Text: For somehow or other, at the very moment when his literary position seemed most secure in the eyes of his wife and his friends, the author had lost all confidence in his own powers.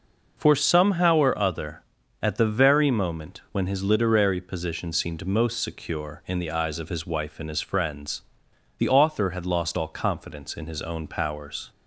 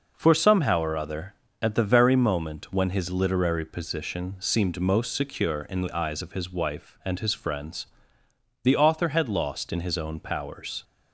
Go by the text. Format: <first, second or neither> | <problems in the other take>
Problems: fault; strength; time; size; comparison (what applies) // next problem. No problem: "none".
first | skips "all confidence"; at 9.7 s